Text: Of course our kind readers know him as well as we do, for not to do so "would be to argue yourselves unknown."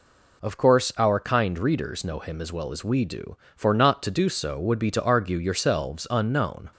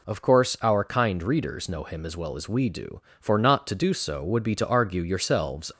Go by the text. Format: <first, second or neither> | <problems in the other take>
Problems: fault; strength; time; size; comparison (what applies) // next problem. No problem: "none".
first | stops before "unknown"; at 5.7 s